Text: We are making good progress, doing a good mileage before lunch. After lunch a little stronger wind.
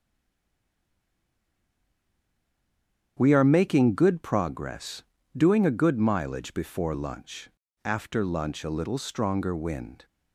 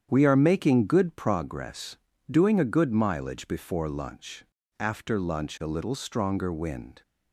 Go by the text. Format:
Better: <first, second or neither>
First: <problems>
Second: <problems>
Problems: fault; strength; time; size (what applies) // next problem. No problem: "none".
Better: second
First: stays silent before the first word; strong; until 3.1 s; 3.1 s long // starts louder than the rest; strong; until 4.2 s; 9 dB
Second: starts louder than the rest; strong; until 1.1 s; 9 dB